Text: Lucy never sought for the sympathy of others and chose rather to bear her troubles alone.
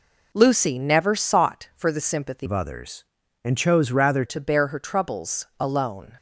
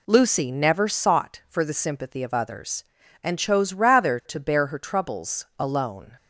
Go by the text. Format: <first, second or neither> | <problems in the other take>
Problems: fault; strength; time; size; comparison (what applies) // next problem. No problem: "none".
second | changes voice from "of" to "rather"; from 2.4 to 4.2 s; 1.8 s long